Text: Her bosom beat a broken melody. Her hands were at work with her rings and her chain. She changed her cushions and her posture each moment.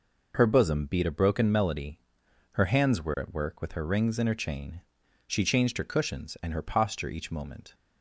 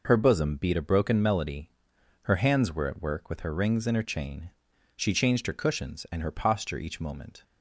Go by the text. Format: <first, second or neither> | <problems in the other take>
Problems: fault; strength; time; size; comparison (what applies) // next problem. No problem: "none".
neither | none